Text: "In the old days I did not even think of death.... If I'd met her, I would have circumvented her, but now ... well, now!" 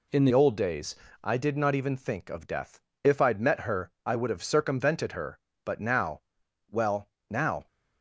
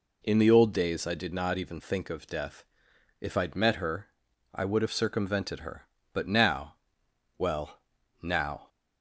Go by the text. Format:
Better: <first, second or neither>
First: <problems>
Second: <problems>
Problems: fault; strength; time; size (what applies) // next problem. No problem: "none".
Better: second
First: changes voice at "old"; from 0.3 s on; 7.3 s long // pauses between "days" and "I"; slight; at 0.9 s; 0.30 s long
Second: none